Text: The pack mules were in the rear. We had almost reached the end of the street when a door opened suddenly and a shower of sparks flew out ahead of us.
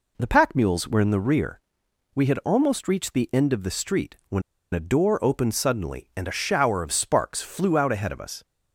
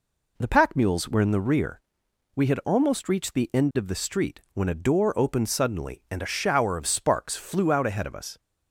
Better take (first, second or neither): second